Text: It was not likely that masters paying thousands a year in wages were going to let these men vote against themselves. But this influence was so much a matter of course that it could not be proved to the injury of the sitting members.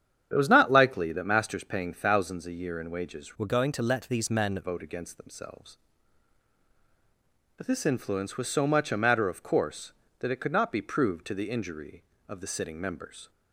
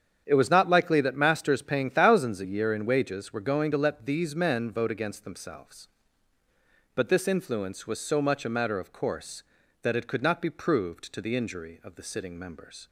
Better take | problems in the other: second | starts louder than the rest; strong; until 1.3 s; 9 dB; strong in the second // changes voice from "were" to "men"; from 3.3 to 4.5 s; 1.2 s long

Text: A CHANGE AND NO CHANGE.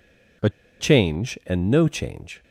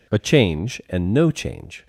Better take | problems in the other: second | pauses between "A" and "CHANGE"; slight; at 0.4 s; 0.31 s long

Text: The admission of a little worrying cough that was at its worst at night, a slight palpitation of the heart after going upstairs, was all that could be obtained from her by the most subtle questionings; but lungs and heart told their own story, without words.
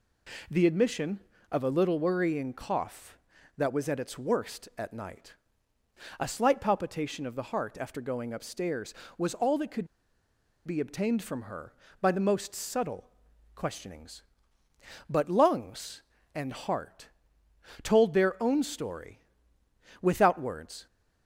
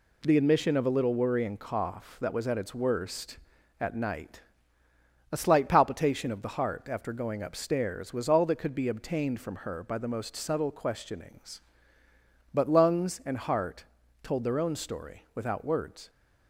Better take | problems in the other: second | pauses between "could" and "be"; noticeable; at 9.8 s; 0.79 s long // pauses between "subtle" and "questionings"; noticeable; at 13.0 s; 0.46 s long // pauses between "heart" and "told"; noticeable; at 17.0 s; 0.74 s long; slight in the second

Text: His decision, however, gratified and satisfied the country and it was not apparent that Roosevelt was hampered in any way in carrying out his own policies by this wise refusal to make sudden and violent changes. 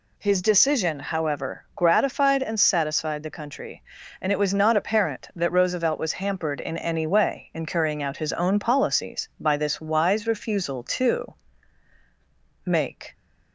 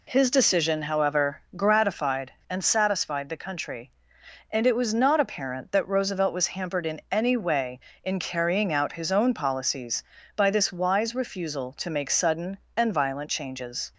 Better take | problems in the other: second | pauses between "to" and "make"; strong; at 11.3 s; 1.3 s long // stops before "sudden and violent changes"; at 13.1 s

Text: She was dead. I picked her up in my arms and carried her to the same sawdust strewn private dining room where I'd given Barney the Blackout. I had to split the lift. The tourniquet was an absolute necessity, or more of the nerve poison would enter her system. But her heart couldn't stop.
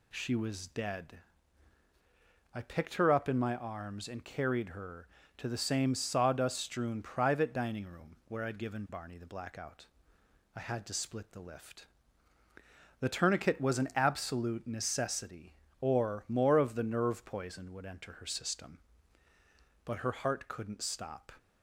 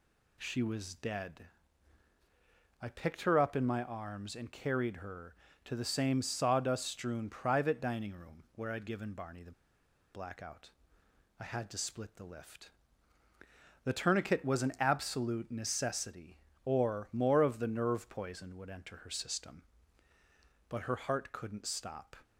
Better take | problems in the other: first | pauses between "the" and "Blackout"; noticeable; at 9.5 s; 0.61 s long

